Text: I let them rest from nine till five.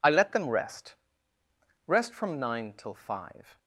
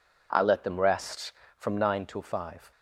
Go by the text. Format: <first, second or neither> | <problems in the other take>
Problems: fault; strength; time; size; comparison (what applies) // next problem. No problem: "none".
second | says "rest" twice; at 1.8 s